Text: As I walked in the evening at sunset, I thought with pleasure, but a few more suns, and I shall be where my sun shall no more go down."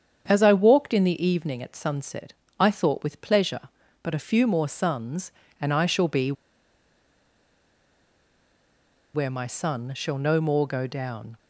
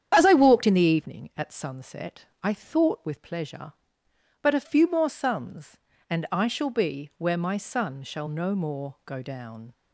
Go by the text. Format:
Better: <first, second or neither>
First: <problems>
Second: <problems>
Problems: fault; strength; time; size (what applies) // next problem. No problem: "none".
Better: second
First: starts louder than the rest; strong; until 1.2 s; 8 dB // pauses between "be" and "where"; strong; at 6.3 s; 2.8 s long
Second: starts louder than the rest; strong; until 1.1 s; 9 dB